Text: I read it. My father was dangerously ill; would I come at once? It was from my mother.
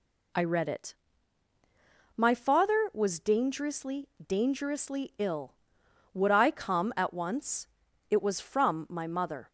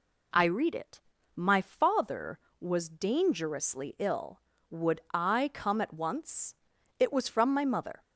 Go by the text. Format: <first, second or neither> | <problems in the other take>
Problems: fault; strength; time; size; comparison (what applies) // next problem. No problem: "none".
second | says "dangerously" twice; at 4.2 s